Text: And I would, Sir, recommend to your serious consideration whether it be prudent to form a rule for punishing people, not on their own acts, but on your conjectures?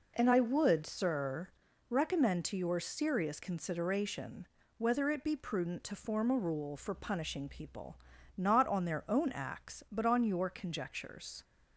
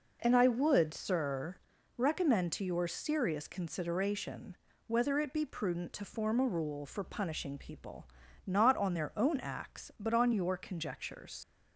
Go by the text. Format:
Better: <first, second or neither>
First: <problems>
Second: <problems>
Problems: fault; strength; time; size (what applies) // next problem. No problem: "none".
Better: first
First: pauses between "consideration" and "whether"; slight; at 4.4 s; 0.32 s long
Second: pauses between "consideration" and "whether"; slight; at 4.5 s; 0.32 s long // leaves "conjectures" unfinished; at 11.4 s; 75 ms